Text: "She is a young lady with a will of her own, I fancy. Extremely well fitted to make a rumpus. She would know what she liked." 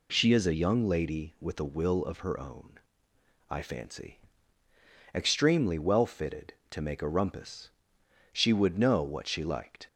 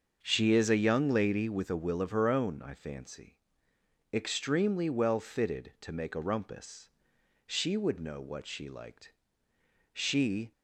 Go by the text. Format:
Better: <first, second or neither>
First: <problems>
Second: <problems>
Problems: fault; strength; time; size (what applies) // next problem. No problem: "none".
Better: first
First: none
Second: starts louder than the rest; until 1.2 s; 6.5 dB // goes on to say "She"; from 9.9 s on; 0.58 s long